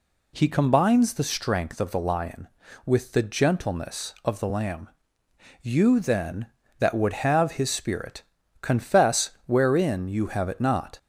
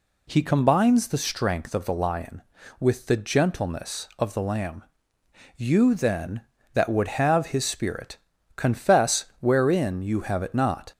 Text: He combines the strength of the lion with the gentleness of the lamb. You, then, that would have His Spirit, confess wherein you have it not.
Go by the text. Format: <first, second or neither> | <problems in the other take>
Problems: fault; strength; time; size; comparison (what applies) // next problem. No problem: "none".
neither | pauses between "confess" and "wherein"; slight; the same in both